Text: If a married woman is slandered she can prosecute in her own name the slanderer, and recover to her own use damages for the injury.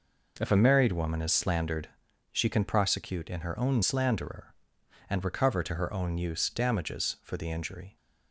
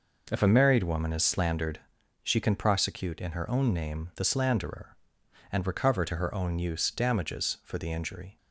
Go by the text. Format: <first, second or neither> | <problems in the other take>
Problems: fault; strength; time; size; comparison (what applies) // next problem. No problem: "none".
second | pauses between "slandered" and "she"; at 1.8 s; 0.42 s long; also in the second // skips "name the"; at 3.8 s